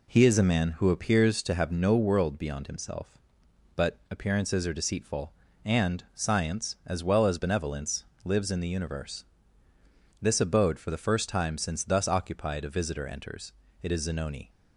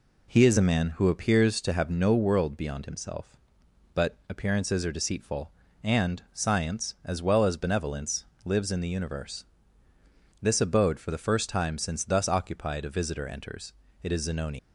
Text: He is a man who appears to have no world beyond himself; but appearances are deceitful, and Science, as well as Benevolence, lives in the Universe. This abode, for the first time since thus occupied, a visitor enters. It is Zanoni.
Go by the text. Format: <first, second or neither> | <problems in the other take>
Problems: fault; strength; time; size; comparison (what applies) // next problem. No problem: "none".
first | leaves "Zanoni" unfinished; at 14.5 s; 105 ms